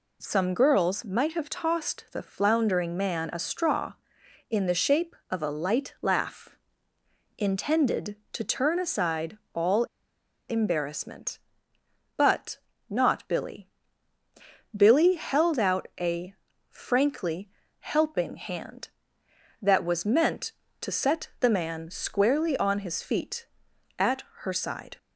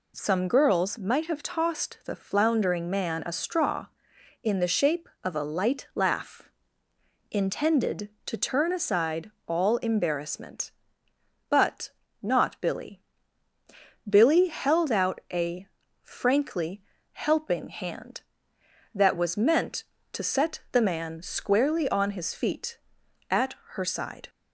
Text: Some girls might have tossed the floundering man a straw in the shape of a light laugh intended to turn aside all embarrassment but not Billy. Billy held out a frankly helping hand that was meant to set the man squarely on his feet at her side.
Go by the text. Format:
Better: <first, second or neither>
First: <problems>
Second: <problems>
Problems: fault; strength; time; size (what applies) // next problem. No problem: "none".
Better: second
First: pauses between "laugh" and "intended"; noticeable; at 6.5 s; 0.82 s long // pauses between "aside" and "all"; slight; at 9.3 s; 0.16 s long // pauses between "all" and "embarrassment"; noticeable; at 9.8 s; 0.63 s long // pauses between "but" and "not"; slight; at 12.5 s; 0.32 s long // pauses between "a" and "frankly"; at 16.3 s; 0.38 s long // pauses between "frankly" and "helping"; slight; at 17.4 s; 0.34 s long // pauses between "at" and "her"; slight; at 24.2 s; 0.16 s long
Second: pauses between "laugh" and "intended"; noticeable; at 6.5 s; 0.82 s long // pauses between "aside" and "all"; slight; at 9.3 s; 0.16 s long // pauses between "but" and "not"; slight; at 11.9 s; 0.32 s long // pauses between "a" and "frankly"; at 15.6 s; 0.38 s long // pauses between "frankly" and "helping"; slight; at 16.8 s; 0.34 s long // pauses between "at" and "her"; slight; at 23.5 s; 0.16 s long